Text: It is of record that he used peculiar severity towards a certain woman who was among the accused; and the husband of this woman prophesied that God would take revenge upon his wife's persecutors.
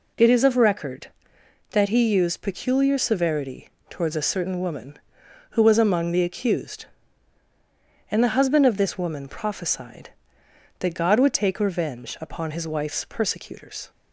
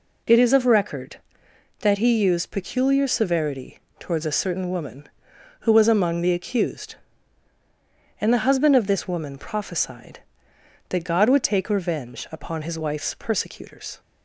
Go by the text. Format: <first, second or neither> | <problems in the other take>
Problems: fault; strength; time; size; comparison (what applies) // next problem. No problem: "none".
neither | pauses between "severity" and "towards"; slight; the same in both